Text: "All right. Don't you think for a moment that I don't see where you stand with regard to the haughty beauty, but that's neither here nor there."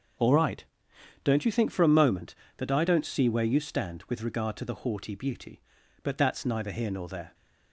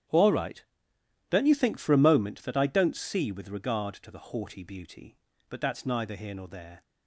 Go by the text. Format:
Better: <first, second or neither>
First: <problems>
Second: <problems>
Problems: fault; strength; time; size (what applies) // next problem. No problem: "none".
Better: first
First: none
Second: starts louder than the rest; strong; until 1.7 s; 10.5 dB // skips "where you stand"; at 3.3 s